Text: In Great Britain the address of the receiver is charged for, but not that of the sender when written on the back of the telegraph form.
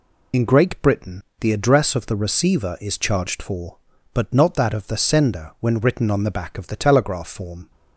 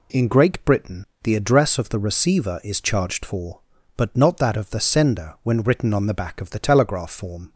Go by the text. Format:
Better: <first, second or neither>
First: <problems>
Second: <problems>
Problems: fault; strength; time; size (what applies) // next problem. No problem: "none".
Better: second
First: loses the start of "In"; at 0.3 s; 70 ms // pauses between "Britain" and "the"; slight; at 1.2 s; 0.18 s long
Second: pauses between "Britain" and "the"; slight; at 1.0 s; 0.18 s long